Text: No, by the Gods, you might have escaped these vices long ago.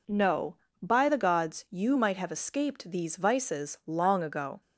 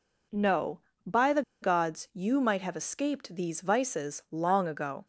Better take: first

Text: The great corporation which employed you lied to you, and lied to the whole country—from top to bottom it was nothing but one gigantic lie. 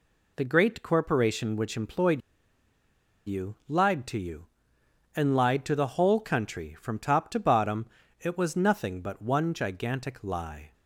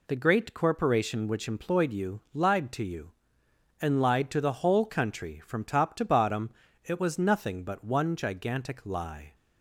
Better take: second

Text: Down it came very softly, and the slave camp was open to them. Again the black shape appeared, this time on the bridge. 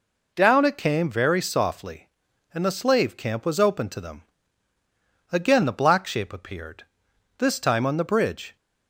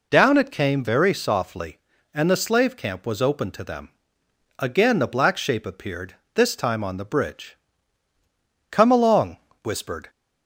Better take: first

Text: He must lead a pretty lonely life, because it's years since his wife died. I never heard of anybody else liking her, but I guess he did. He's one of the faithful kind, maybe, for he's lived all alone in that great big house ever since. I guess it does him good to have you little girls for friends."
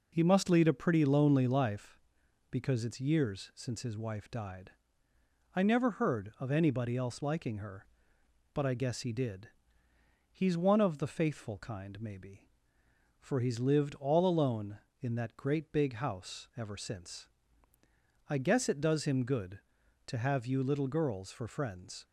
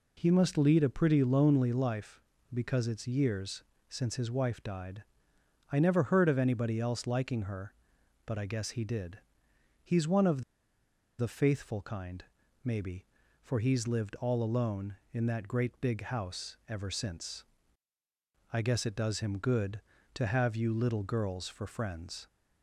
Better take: first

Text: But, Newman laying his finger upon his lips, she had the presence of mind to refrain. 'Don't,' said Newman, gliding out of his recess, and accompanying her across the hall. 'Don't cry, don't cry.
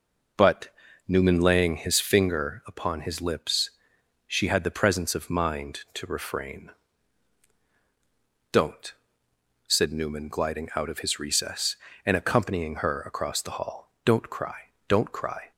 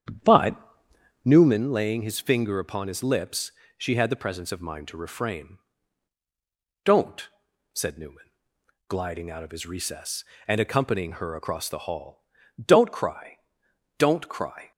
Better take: first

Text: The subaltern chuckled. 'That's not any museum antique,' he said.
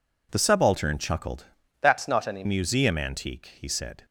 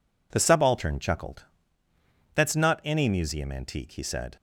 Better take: second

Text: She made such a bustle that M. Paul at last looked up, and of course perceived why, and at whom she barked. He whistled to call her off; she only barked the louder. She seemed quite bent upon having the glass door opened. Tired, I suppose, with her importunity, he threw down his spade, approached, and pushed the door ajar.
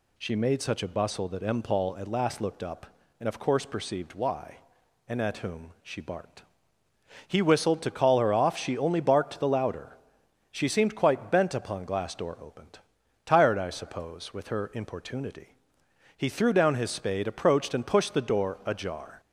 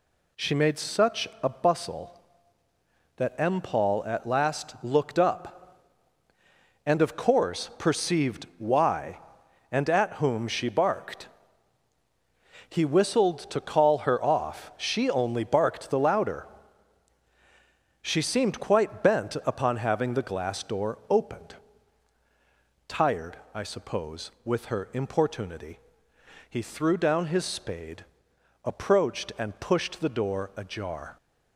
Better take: second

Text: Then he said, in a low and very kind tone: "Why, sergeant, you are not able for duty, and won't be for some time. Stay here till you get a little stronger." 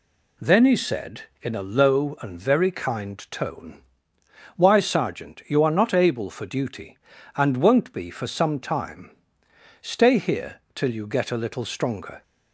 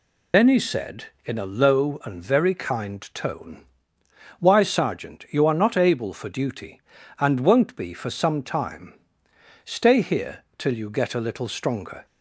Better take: first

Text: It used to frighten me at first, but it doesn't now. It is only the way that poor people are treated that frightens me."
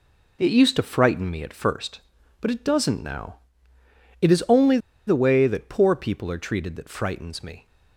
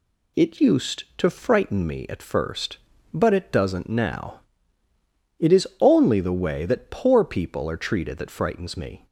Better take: second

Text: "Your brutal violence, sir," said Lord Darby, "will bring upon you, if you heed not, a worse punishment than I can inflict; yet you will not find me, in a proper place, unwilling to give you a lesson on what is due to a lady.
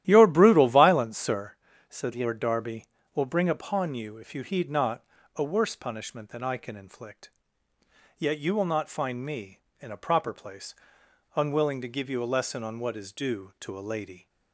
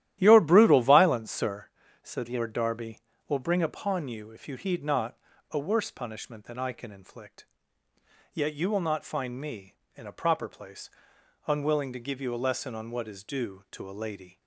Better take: neither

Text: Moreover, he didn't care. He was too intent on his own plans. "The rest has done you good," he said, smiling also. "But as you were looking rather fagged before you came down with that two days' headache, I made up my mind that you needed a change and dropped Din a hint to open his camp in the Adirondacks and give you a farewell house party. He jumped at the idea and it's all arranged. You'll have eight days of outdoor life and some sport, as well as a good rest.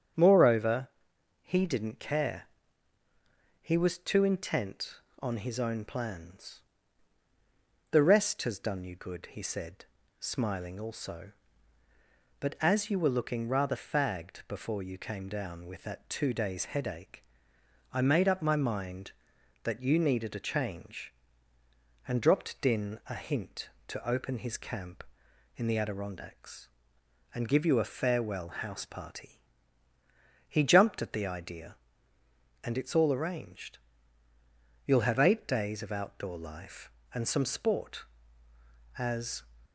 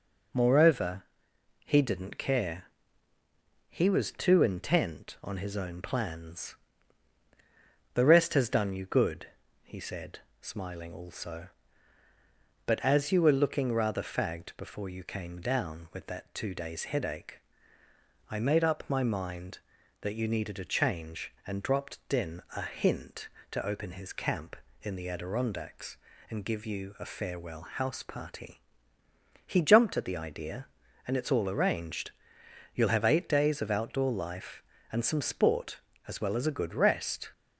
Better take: second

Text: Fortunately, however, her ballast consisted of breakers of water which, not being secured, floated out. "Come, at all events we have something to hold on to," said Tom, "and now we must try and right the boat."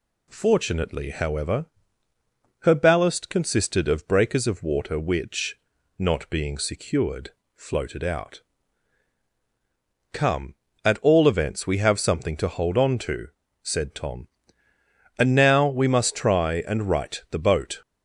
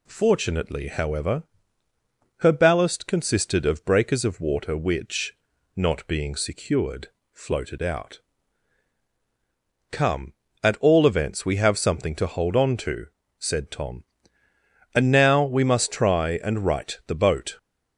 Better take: neither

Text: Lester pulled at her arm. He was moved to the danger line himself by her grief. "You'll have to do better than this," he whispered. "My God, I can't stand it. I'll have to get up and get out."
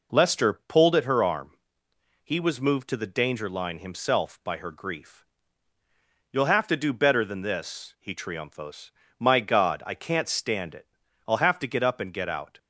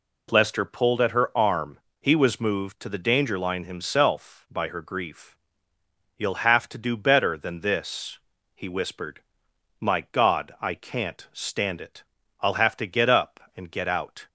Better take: second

